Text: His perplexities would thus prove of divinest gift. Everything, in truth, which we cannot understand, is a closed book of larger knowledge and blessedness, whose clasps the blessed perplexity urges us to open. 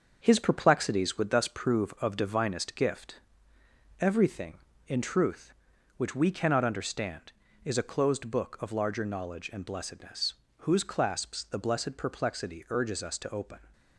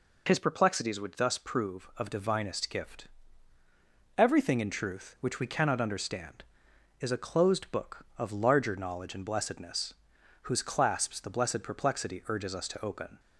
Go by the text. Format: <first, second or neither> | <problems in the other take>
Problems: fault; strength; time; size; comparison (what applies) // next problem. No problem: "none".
second | gets quieter; noticeable; throughout; 5 dB